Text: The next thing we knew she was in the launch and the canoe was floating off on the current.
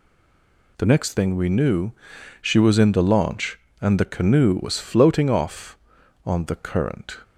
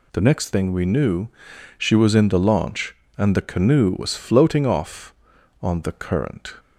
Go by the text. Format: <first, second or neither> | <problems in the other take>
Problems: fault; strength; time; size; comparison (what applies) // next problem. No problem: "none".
second | stays silent before the first word; slight; until 0.7 s; 0.7 s long // pauses between "knew" and "she"; noticeable; at 1.9 s; 0.48 s long; noticeable in the second